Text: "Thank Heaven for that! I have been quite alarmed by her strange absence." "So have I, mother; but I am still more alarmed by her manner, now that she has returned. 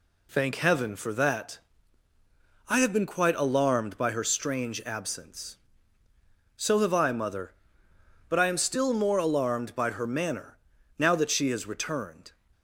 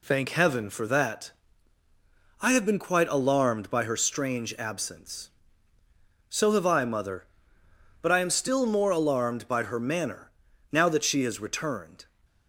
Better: neither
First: none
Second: none

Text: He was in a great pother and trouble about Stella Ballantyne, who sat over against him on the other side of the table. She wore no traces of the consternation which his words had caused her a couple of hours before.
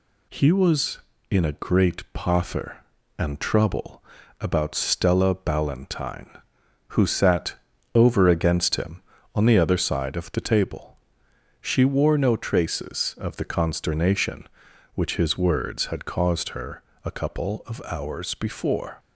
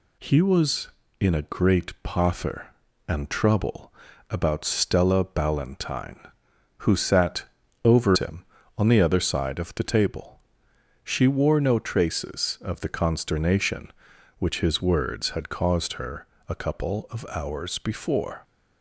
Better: first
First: pauses between "trouble" and "about"; at 4.0 s; 0.38 s long // pauses between "sat" and "over"; at 7.5 s; 0.40 s long // pauses between "her" and "a"; slight; at 16.8 s; 0.24 s long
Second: pauses between "trouble" and "about"; at 3.9 s; 0.38 s long // pauses between "sat" and "over"; at 7.4 s; 0.40 s long // skips "against"; at 8.1 s // pauses between "her" and "a"; slight; at 16.2 s; 0.24 s long

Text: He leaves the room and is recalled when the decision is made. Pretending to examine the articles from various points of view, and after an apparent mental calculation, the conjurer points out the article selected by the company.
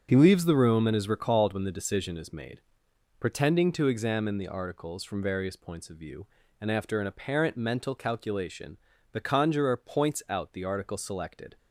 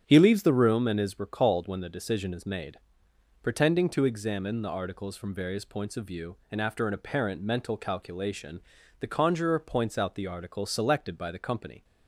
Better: second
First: starts louder than the rest; until 1.1 s; 6.5 dB // stops before "by the company"; at 11.5 s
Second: starts louder than the rest; strong; until 1.0 s; 8 dB

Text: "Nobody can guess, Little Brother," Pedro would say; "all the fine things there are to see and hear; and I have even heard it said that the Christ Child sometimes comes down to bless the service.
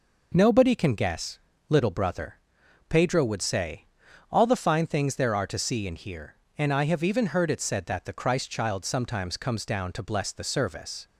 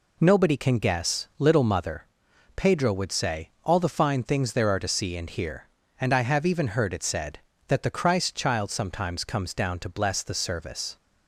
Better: first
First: none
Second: says "Mother" for "Brother"; at 1.6 s

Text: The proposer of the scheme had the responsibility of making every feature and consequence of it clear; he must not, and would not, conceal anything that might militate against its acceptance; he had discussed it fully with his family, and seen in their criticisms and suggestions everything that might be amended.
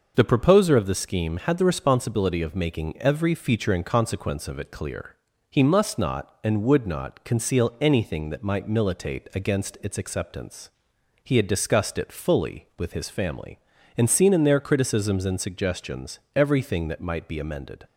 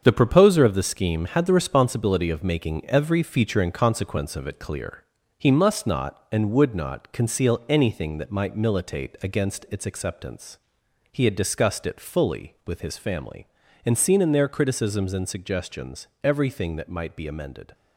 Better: first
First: none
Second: gets quieter; strong; throughout; 7.5 dB

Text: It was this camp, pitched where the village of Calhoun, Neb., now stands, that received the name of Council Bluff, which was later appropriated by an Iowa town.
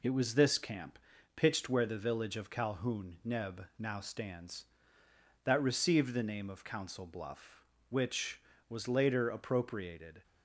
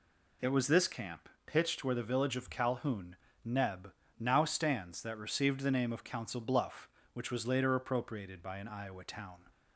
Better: second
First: stops before "by an Iowa town"; at 10.2 s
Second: none

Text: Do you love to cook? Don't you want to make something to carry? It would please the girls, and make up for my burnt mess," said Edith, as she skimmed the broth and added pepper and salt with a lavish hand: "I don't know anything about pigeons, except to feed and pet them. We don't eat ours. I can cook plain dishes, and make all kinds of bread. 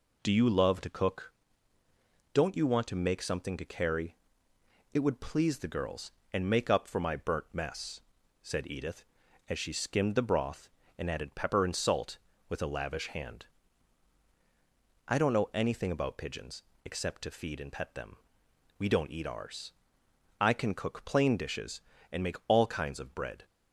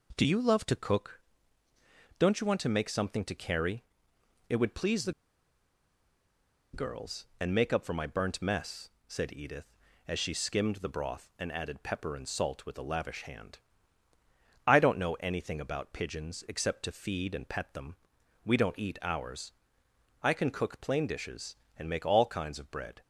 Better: first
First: none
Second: pauses between "the" and "girls"; strong; at 5.1 s; 1.6 s long

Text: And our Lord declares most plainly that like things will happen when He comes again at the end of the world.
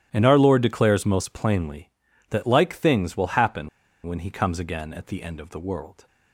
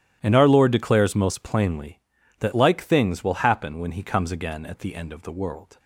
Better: second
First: starts louder than the rest; strong; until 1.1 s; 12 dB // pauses between "happen" and "when"; at 3.6 s; 0.37 s long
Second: starts louder than the rest; strong; until 1.2 s; 12 dB

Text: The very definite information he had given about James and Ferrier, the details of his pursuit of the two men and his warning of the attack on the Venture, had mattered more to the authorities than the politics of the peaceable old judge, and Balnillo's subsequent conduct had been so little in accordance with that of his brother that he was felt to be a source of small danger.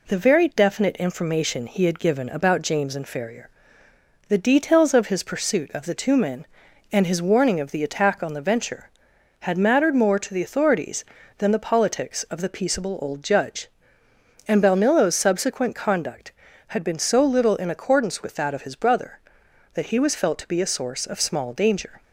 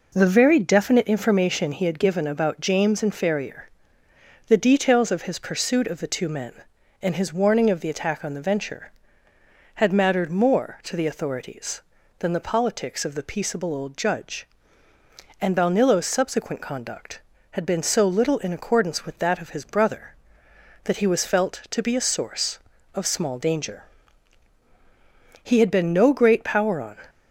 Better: first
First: none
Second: goes on to say "He had been no great power on"; from 25.4 s on; 1.5 s long

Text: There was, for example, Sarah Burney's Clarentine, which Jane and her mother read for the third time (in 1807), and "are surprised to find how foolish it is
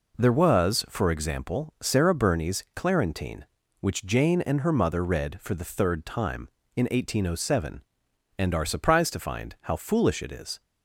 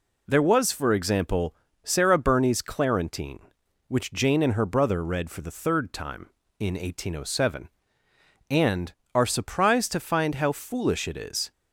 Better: first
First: none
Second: says "brother" for "mother"; at 4.6 s

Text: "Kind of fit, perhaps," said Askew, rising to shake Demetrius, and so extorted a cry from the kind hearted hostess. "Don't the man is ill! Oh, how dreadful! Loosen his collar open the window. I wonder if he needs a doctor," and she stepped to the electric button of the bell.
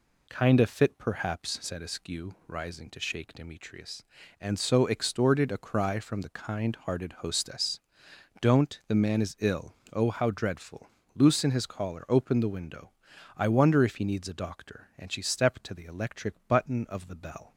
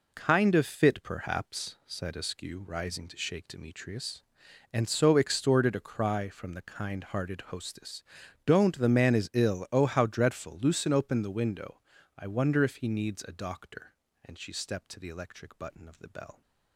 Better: first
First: none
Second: skips "his collar"; at 10.9 s

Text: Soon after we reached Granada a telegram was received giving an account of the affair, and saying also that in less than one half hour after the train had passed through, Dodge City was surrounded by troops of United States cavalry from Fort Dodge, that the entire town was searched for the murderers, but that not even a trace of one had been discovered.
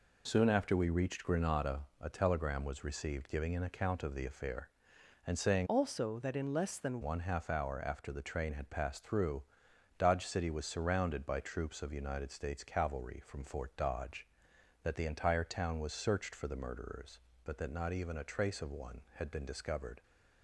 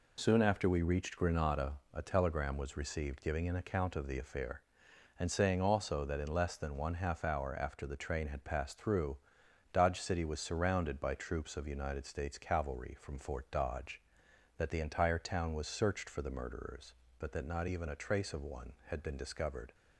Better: second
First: pauses between "Granada" and "a"; slight; at 1.8 s; 0.16 s long // changes voice from "also" to "than"; from 5.6 to 7.0 s; 1.4 s long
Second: pauses between "Granada" and "a"; slight; at 1.7 s; 0.16 s long

